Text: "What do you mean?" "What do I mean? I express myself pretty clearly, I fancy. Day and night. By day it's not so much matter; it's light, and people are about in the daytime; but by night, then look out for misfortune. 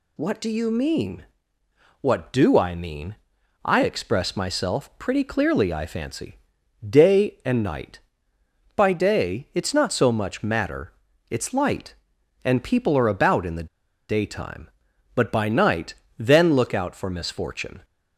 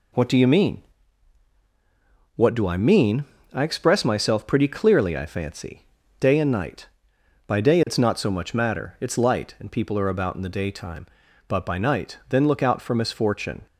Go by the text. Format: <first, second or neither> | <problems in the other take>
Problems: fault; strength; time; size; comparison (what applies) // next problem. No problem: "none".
second | pauses between "the" and "daytime"; at 13.6 s; 0.41 s long